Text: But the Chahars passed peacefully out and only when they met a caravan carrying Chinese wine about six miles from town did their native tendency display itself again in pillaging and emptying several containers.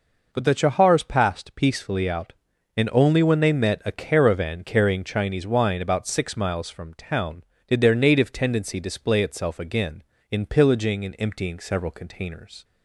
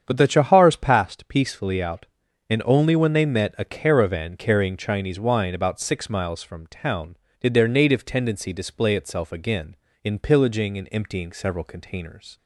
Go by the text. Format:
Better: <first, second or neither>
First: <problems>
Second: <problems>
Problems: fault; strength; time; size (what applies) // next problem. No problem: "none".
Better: first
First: none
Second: starts louder than the rest; strong; until 1.1 s; 8 dB